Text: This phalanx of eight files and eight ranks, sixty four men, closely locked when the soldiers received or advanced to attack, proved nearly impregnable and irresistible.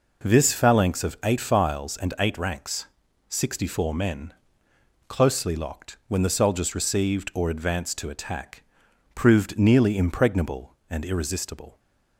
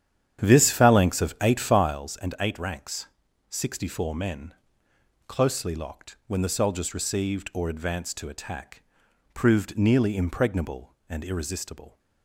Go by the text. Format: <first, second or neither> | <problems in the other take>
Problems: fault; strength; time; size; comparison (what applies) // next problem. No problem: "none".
first | starts louder than the rest; strong; until 2.0 s; 9.5 dB